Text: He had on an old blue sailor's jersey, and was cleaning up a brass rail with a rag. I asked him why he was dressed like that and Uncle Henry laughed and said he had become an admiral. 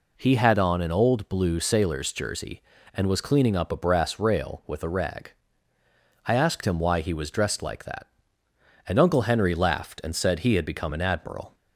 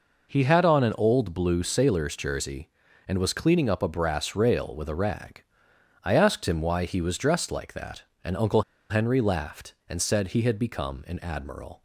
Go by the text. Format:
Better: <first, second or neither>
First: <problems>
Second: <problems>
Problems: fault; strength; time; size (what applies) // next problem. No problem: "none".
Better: first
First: none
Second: pauses between "Uncle" and "Henry"; slight; at 8.6 s; 0.28 s long